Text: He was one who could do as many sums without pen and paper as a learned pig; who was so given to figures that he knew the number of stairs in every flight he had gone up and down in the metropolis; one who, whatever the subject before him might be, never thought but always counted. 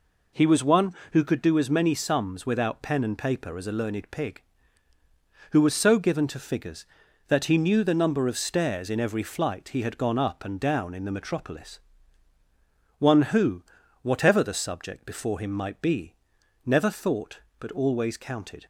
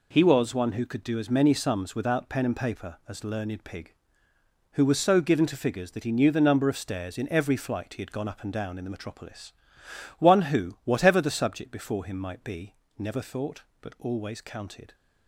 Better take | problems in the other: first | skips "a"; at 3.2 s

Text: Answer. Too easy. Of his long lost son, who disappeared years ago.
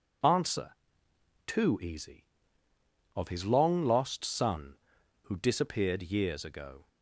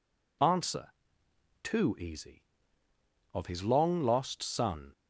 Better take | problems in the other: first | stops before "who disappeared years ago"; at 4.9 s

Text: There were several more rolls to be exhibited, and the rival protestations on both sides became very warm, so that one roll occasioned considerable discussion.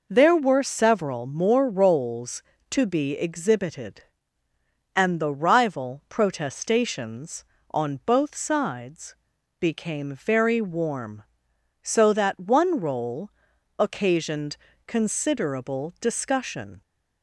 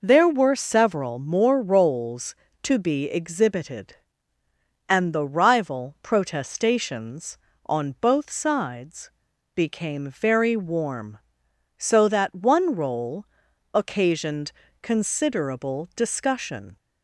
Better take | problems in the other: neither | pauses between "sides" and "became"; noticeable; the same in both // pauses between "roll" and "occasioned"; noticeable; the same in both // pauses between "occasioned" and "considerable"; slight; the same in both

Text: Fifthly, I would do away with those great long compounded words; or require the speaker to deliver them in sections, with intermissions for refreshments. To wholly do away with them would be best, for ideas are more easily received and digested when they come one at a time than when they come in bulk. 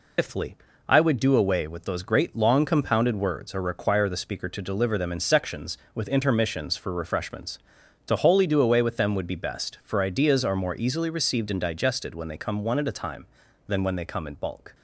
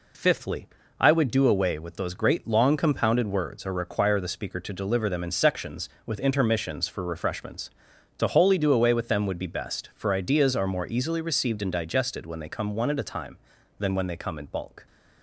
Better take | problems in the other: second | loses the start of "Fifthly"; at 0.1 s; 150 ms

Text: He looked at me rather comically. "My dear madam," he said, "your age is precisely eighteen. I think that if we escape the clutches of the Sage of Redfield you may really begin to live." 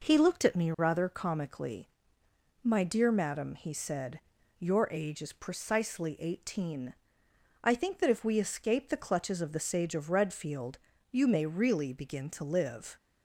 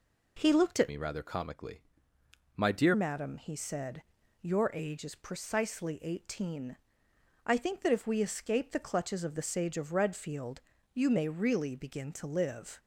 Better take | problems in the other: first | changes voice from "me" to "dear"; from 0.8 to 2.9 s; 2.1 s long // pauses between "Redfield" and "you"; slight; at 10.6 s; 0.32 s long; slight in the first

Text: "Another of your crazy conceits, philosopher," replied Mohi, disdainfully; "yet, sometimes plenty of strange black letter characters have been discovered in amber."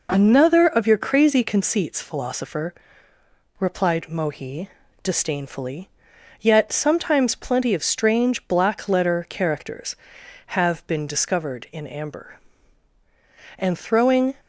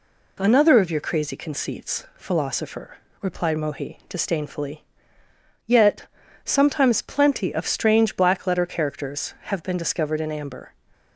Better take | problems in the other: second | goes on to say "And throwing"; noticeable; from 13.5 s on; 0.78 s long

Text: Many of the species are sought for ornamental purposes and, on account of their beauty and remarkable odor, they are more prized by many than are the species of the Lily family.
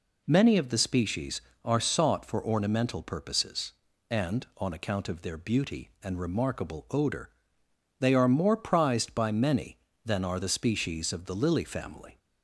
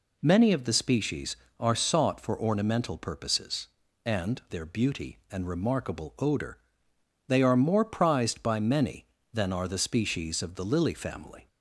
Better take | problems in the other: first | skips "on account of"; at 4.4 s

